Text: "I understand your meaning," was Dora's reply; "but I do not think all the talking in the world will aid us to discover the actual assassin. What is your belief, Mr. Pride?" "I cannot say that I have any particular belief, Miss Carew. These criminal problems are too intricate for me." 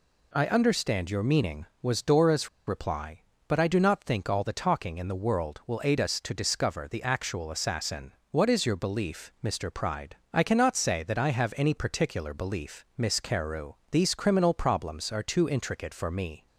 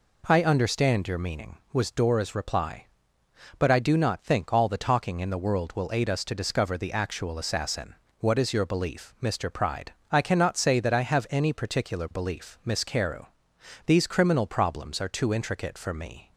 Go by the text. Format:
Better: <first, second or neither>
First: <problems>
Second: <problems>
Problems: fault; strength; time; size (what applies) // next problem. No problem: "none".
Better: second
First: pauses between "Dora's" and "reply"; slight; at 2.4 s; 0.18 s long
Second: none